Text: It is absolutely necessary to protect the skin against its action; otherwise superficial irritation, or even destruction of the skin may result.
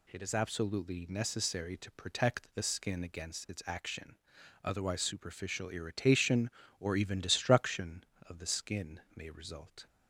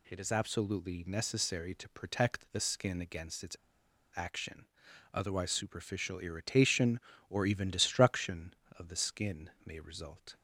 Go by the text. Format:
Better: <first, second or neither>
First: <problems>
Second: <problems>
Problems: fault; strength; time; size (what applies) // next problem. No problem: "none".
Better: first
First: pauses between "skin" and "may"; slight; at 8.9 s; 0.16 s long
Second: pauses between "its" and "action"; noticeable; at 3.5 s; 0.59 s long // pauses between "skin" and "may"; slight; at 9.4 s; 0.16 s long